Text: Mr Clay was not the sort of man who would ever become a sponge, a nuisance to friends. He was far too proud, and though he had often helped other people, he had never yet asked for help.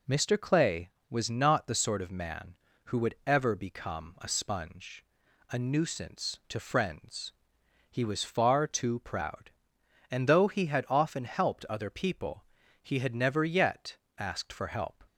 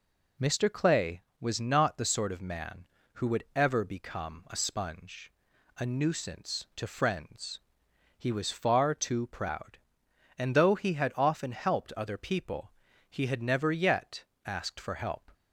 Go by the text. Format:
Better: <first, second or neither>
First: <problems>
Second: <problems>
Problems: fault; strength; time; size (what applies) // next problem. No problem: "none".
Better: neither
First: pauses between "yet" and "asked"; slight; at 13.9 s; 0.20 s long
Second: pauses between "yet" and "asked"; slight; at 14.2 s; 0.20 s long